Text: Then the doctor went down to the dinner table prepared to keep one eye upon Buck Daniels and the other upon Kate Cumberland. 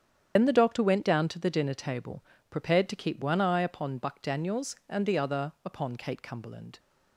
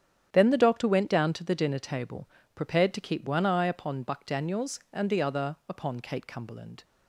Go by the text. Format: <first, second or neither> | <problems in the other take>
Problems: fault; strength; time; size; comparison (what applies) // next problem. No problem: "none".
second | loses the start of "Then"; at 0.3 s; 75 ms // starts louder than the rest; strong; until 1.3 s; 8.5 dB; strong in the second // pauses between "table" and "prepared"; slight; at 2.2 s; 0.26 s long; slight in the second